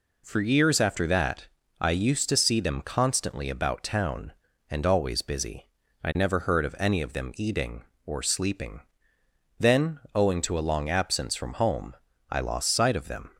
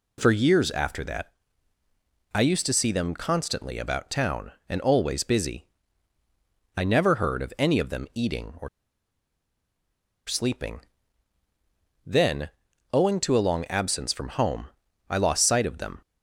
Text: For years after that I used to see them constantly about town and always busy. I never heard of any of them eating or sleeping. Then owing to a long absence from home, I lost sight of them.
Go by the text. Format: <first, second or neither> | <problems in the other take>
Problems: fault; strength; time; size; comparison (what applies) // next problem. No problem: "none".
first | pauses between "that" and "I"; at 1.3 s; 1.0 s long; slight in the first // pauses between "or" and "sleeping"; strong; at 8.6 s; 1.5 s long // pauses between "Then" and "owing"; at 12.4 s; 0.42 s long